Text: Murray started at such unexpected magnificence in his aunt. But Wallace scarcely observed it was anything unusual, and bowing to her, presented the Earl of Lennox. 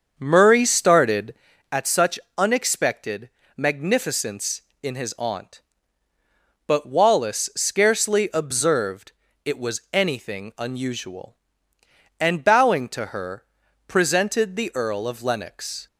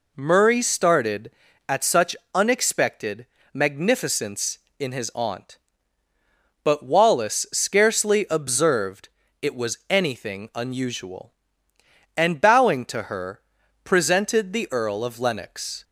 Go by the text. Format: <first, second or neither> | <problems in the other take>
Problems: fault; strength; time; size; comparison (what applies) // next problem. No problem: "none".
second | starts louder than the rest; until 1.5 s; 7 dB // pauses between "such" and "unexpected"; slight; at 2.1 s; 0.20 s long; slight in the second // pauses between "unexpected" and "magnificence"; slight; at 3.2 s; 0.28 s long; slight in the second // pauses between "observed" and "it"; slight; at 9.1 s; 0.32 s long; slight in the second